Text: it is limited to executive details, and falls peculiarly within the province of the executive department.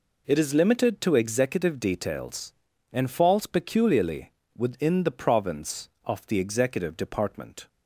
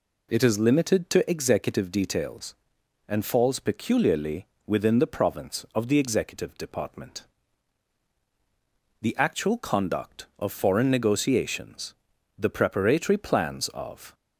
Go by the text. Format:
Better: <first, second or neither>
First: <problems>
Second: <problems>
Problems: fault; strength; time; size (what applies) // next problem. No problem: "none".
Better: first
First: pauses between "peculiarly" and "within"; slight; at 4.3 s; 0.24 s long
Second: pauses between "peculiarly" and "within"; slight; at 4.4 s; 0.20 s long // goes on to say "The actual conduct of foreign negotiations the preparatory plans of"; strong; from 9.0 s on; 5.1 s long